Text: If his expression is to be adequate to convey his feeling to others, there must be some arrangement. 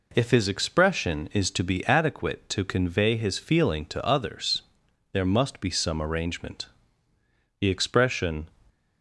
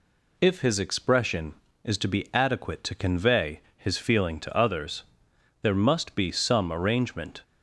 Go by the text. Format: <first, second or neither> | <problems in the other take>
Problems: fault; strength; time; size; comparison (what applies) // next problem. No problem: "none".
second | goes on to say "The expression"; noticeable; from 7.6 s on; 0.88 s long